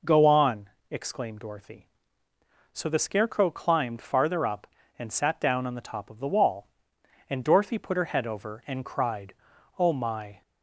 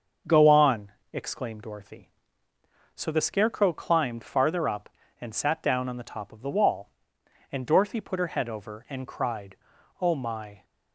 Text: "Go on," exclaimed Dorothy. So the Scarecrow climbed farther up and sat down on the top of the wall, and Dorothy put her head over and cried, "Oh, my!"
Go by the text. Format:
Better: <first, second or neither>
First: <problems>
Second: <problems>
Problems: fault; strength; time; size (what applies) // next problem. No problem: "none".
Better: first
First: none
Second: gets quieter; throughout; 3.5 dB